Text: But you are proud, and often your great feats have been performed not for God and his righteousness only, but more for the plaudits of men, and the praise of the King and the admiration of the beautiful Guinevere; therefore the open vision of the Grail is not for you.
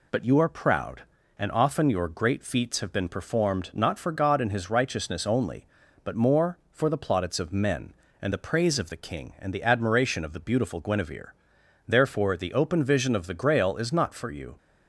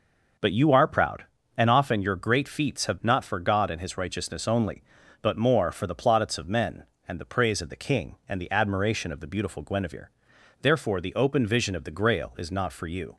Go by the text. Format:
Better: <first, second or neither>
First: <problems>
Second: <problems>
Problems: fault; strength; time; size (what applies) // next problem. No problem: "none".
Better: first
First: none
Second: skips "been performed"; at 3.0 s